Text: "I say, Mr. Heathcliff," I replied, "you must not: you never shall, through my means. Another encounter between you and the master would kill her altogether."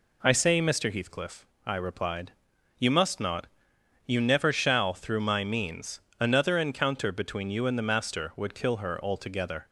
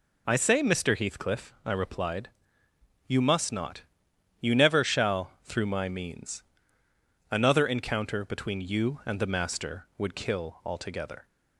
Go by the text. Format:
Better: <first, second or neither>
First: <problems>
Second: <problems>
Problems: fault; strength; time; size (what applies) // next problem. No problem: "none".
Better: first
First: none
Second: skips "her"; at 10.6 s